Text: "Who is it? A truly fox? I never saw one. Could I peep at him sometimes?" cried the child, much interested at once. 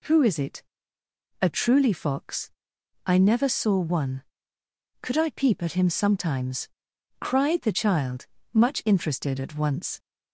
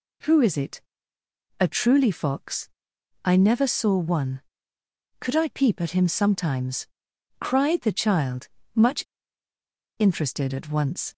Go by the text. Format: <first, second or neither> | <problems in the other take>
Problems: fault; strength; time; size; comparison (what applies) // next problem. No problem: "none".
first | pauses between "much" and "interested"; noticeable; at 9.0 s; 0.96 s long